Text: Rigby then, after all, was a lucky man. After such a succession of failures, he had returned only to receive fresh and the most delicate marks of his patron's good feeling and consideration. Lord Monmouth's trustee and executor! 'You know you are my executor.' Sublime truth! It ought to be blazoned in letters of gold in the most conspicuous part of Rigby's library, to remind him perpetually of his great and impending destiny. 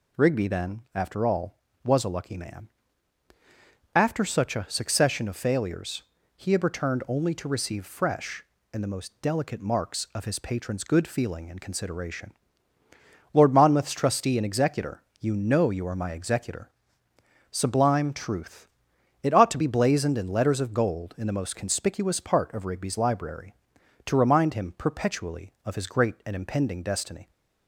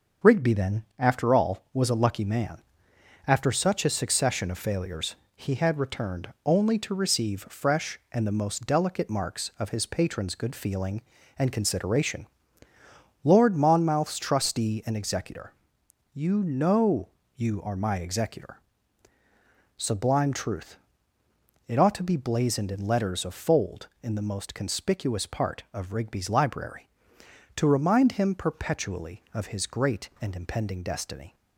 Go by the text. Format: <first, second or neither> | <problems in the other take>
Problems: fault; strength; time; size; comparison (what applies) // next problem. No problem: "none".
first | pauses between "returned" and "only"; slight; at 6.2 s; 0.16 s long // pauses between "know" and "you"; slight; at 17.0 s; 0.26 s long // says "fold" for "gold"; at 23.3 s